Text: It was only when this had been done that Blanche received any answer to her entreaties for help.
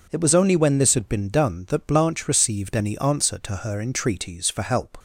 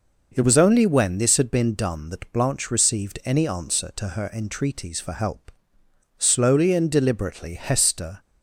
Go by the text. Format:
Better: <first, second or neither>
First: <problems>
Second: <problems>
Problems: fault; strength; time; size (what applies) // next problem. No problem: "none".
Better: first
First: none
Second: goes on to say "Slowly and deliberately Hester"; strong; from 6.1 s on; 2.0 s long